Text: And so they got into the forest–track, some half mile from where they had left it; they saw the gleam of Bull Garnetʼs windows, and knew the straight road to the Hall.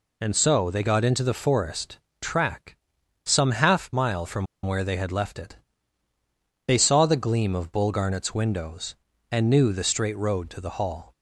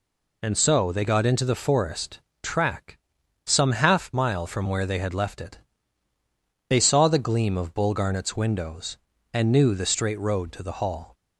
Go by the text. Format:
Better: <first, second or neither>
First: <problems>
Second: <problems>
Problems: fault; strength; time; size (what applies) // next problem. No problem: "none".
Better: second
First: pauses between "from" and "where"; slight; at 4.4 s; 0.19 s long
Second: none